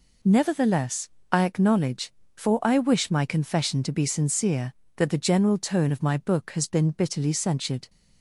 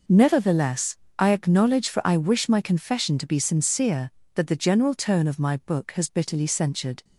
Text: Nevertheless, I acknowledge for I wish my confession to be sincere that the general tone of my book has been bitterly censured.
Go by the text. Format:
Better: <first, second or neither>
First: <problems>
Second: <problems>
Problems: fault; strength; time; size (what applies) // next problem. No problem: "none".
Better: first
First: none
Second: skips "been"; at 6.0 s